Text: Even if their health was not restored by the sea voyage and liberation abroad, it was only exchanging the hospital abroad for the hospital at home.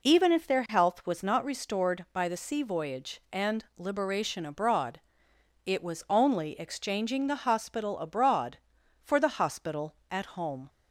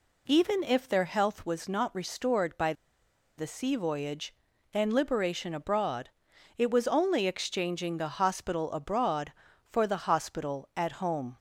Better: first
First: none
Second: pauses between "by" and "the"; noticeable; at 2.7 s; 0.65 s long

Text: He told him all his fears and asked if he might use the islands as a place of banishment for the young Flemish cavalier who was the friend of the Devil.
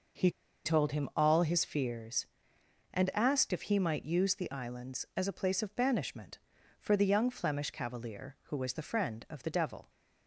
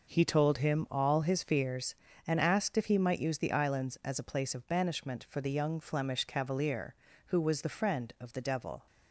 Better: second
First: pauses between "He" and "told"; slight; at 0.3 s; 0.34 s long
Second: none

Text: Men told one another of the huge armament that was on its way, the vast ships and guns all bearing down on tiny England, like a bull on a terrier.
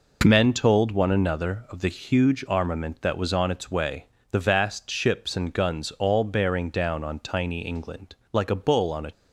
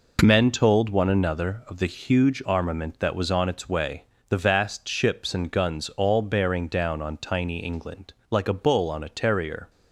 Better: second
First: stops before "terrier"; at 9.1 s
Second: none

